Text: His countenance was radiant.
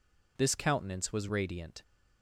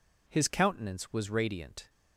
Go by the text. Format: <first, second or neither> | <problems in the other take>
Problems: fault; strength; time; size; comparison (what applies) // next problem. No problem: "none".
second | says "This" for "His"; at 0.3 s